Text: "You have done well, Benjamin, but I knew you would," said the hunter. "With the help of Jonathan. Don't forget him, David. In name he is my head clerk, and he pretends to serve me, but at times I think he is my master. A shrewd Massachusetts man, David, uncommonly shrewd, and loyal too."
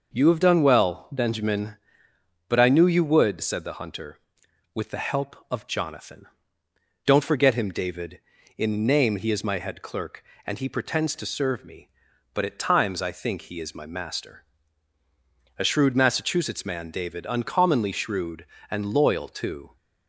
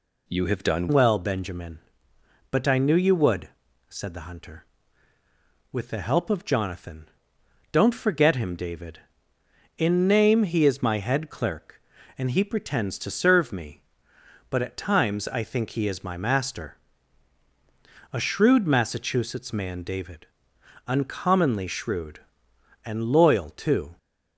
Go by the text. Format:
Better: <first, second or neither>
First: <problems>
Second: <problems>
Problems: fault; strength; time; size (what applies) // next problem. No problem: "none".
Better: first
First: none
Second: changes voice at "well"; from 0.8 s on; 23.1 s long